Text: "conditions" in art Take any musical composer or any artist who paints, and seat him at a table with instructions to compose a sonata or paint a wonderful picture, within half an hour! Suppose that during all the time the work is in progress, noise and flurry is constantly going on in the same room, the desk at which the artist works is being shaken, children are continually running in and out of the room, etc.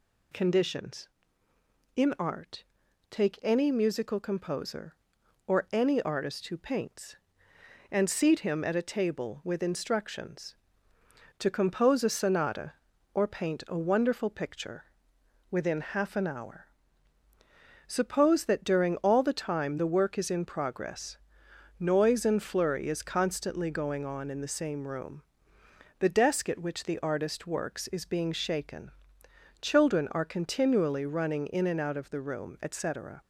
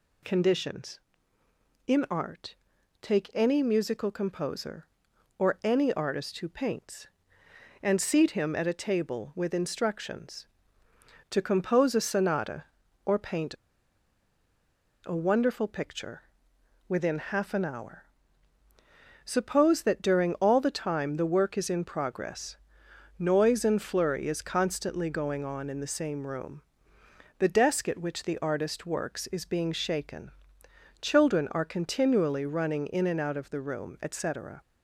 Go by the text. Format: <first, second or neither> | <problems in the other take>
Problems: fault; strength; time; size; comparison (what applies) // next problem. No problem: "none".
first | pauses between "art" and "Take"; noticeable; at 2.5 s; 0.46 s long; noticeable in the first // pauses between "paint" and "a"; strong; at 13.5 s; 1.5 s long